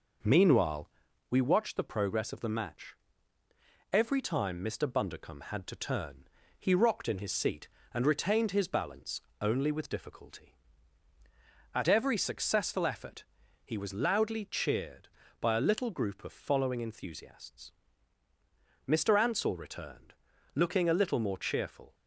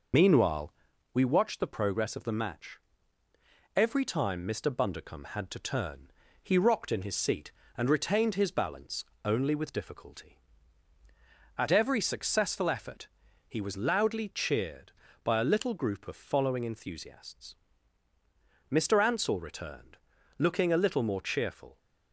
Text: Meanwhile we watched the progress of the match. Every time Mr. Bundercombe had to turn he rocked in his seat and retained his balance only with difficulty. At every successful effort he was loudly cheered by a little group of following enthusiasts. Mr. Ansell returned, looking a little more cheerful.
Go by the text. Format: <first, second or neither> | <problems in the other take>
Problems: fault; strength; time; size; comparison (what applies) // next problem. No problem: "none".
first | loses the start of "Meanwhile"; at 0.1 s; 80 ms // pauses between "Meanwhile" and "we"; at 0.7 s; 0.42 s long; also in the first // pauses between "turn" and "he"; slight; at 6.0 s; 0.32 s long; slight in the first // pauses between "balance" and "only"; slight; at 9.0 s; 0.18 s long; slight in the first // pauses between "effort" and "he"; at 13.0 s; 0.40 s long; also in the first